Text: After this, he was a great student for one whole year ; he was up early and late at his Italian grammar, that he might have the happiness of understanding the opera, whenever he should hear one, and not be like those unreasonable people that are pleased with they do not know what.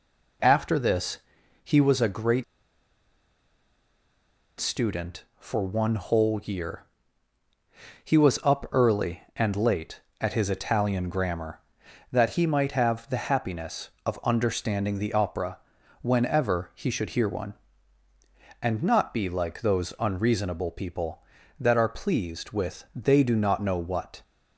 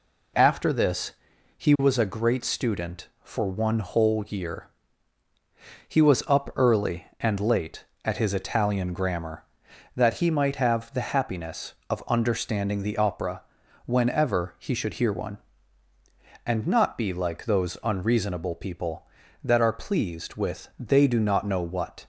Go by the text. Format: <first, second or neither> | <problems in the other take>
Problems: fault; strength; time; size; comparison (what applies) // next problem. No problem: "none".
second | pauses between "great" and "student"; strong; at 2.4 s; 2.1 s long